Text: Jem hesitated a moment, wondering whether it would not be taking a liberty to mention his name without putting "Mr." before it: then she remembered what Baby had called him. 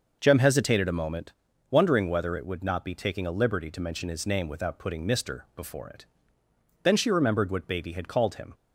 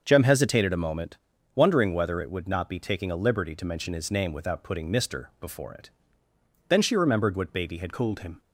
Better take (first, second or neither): first